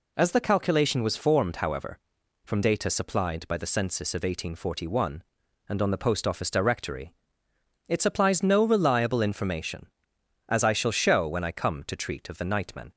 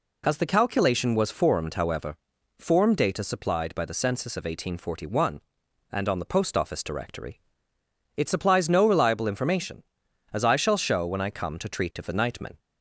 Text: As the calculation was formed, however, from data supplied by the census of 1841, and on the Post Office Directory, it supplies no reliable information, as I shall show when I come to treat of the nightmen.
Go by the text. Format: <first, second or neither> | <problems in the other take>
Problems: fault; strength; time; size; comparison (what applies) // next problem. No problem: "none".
first | says "form" for "from"; at 2.5 s